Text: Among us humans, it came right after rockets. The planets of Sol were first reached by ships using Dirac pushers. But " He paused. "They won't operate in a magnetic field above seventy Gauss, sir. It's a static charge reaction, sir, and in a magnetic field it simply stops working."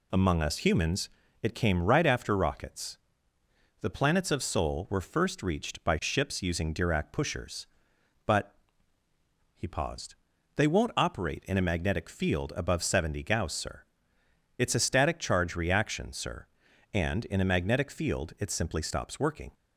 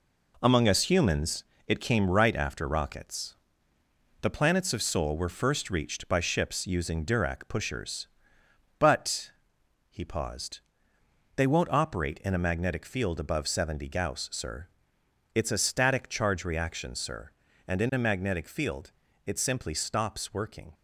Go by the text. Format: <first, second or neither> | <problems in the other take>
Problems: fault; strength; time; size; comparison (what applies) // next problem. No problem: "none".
first | gets quieter; throughout; 6.5 dB // pauses between "field" and "it"; slight; at 18.9 s; 0.34 s long